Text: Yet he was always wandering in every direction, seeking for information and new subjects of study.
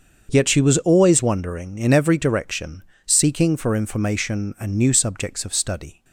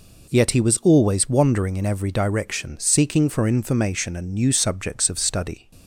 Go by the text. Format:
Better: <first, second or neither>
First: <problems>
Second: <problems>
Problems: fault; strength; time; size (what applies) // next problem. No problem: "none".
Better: second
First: starts louder than the rest; until 1.3 s; 7 dB // says "she" for "he"; at 0.4 s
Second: none